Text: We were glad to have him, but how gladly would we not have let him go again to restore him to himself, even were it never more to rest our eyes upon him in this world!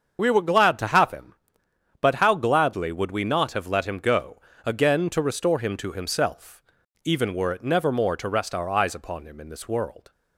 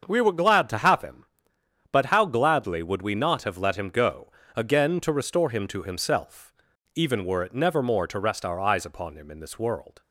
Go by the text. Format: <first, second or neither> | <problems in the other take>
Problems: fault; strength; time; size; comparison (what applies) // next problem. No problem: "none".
second | loses the start of "We"; at 0.1 s; 70 ms // starts louder than the rest; until 1.2 s; 7 dB; also in the second // pauses between "go" and "again"; slight; at 4.3 s; 0.26 s long; slight in the second